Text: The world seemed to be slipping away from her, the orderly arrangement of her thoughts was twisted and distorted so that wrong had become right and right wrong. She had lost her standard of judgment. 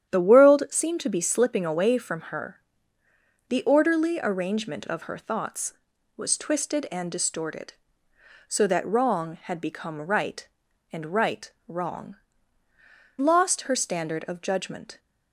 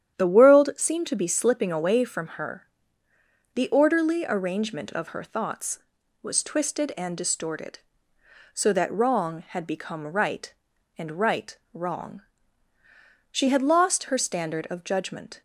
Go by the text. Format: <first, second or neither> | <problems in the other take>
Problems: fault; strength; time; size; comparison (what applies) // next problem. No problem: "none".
second | starts louder than the rest; strong; until 1.1 s; 9.5 dB; strong in the second // pauses between "right" and "wrong"; slight; at 11.5 s; 0.16 s long; slight in the second // skips "She had"; at 12.6 s